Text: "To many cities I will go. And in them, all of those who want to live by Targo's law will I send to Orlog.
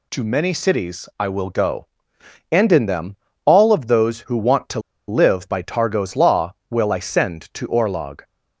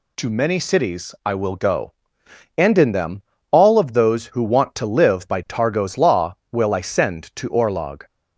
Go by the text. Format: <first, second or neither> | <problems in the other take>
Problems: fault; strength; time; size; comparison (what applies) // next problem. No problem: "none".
second | pauses between "to" and "live"; slight; at 4.7 s; 0.29 s long